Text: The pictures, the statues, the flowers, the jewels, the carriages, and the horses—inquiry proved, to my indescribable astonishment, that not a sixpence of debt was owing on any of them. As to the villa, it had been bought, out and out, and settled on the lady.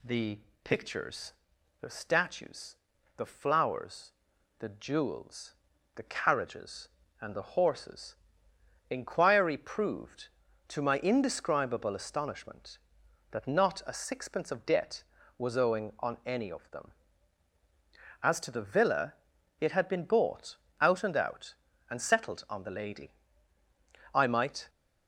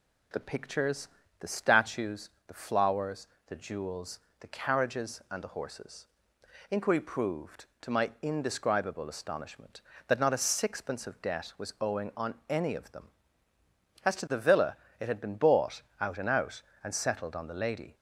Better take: second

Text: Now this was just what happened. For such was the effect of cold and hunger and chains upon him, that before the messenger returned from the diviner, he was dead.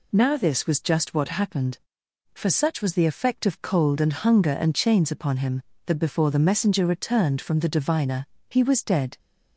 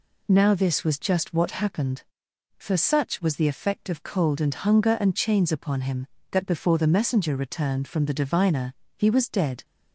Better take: neither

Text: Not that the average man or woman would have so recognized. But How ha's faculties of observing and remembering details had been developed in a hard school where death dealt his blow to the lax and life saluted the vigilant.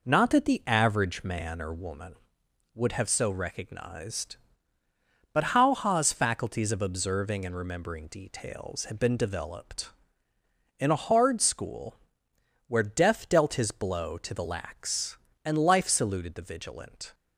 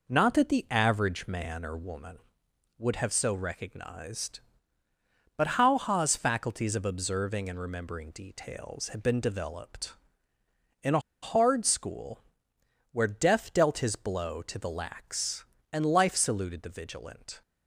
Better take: first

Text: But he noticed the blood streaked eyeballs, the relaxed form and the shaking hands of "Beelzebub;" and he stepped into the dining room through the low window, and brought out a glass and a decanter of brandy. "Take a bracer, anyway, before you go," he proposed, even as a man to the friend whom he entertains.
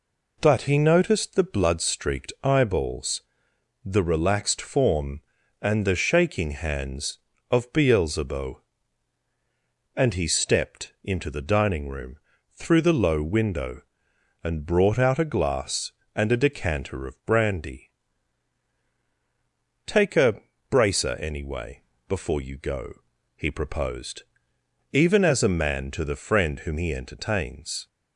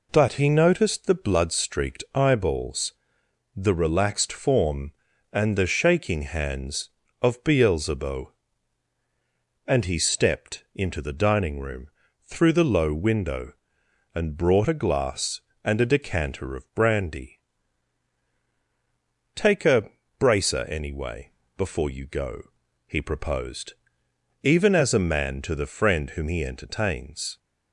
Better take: first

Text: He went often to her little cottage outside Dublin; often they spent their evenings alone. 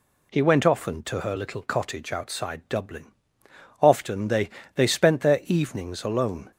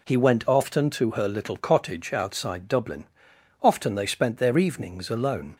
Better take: second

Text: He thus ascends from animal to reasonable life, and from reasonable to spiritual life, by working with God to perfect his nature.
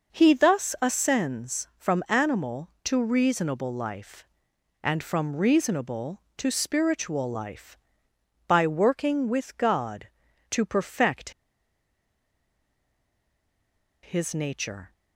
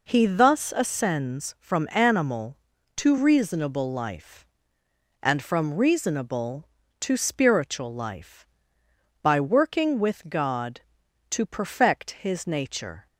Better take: second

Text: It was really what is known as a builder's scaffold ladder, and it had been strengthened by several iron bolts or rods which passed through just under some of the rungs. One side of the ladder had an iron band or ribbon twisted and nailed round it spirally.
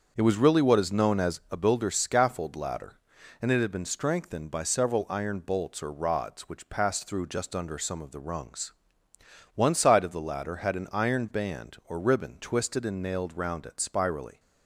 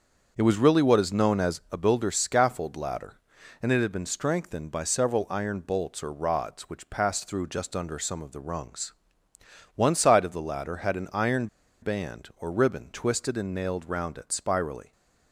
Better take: first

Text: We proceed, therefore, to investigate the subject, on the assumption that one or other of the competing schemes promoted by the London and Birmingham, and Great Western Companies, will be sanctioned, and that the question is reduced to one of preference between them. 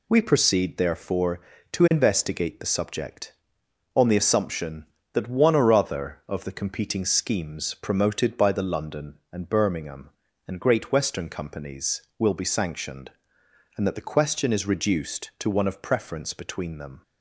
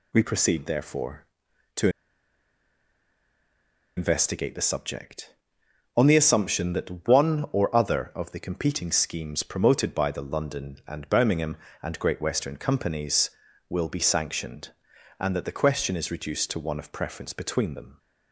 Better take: first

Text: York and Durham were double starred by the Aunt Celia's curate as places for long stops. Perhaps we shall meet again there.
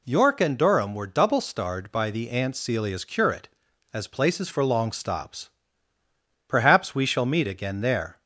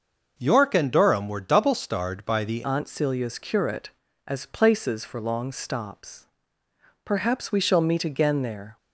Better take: first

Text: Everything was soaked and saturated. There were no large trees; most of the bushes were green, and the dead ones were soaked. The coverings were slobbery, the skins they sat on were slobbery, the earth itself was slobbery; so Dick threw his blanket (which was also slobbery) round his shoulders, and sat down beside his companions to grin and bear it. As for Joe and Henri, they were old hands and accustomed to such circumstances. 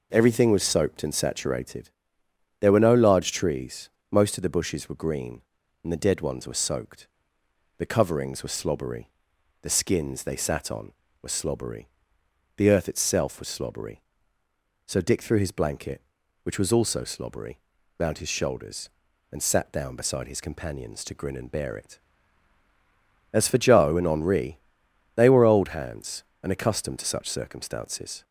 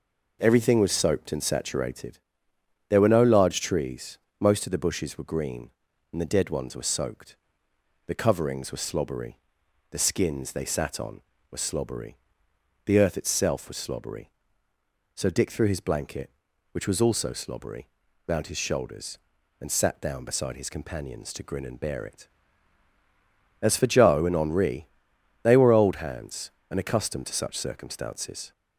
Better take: neither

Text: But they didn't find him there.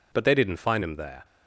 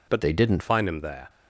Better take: first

